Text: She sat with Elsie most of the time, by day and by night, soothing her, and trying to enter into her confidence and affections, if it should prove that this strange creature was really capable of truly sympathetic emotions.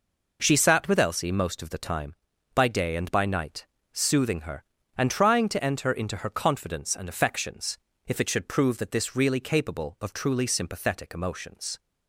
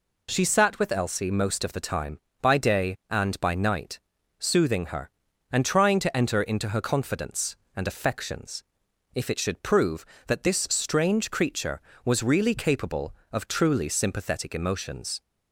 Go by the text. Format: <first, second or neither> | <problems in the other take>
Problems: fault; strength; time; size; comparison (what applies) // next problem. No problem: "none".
second | skips "strange creature was"; at 9.1 s